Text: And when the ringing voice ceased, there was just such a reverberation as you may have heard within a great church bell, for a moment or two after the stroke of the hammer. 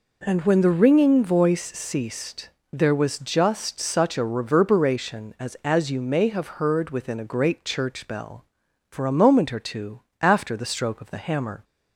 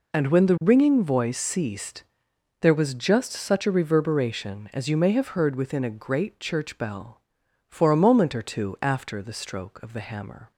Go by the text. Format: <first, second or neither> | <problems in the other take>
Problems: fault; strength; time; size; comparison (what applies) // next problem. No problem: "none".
second | says "as" twice; at 5.6 s // pauses between "two" and "after"; slight; at 10.0 s; 0.18 s long